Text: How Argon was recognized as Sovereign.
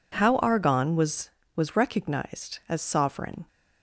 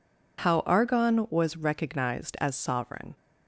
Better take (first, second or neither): second